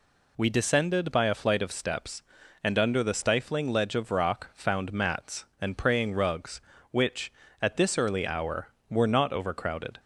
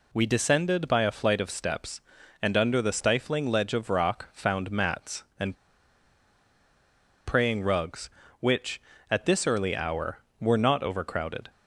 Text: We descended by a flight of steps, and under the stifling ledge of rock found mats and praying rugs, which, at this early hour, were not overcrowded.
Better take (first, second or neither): first